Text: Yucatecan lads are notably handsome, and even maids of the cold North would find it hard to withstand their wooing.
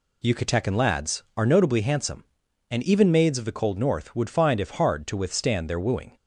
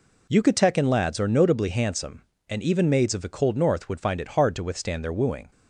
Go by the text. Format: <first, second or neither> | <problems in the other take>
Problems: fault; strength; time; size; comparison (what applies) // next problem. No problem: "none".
second | says "if" for "it"; at 4.5 s